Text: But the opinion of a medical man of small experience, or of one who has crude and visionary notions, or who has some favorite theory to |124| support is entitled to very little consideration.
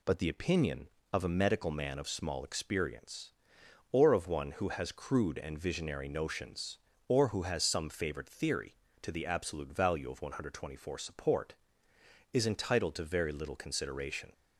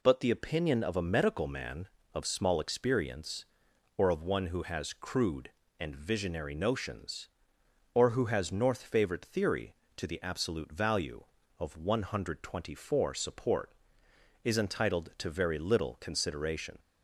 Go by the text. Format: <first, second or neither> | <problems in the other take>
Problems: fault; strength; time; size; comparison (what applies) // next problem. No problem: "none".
first | says "north" for "some"; at 8.5 s